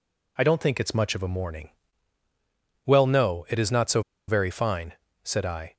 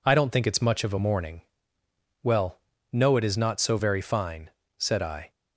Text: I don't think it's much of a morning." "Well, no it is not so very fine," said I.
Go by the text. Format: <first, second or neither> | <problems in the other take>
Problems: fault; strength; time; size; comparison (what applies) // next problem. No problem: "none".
second | pauses between "so" and "very"; slight; at 4.0 s; 0.27 s long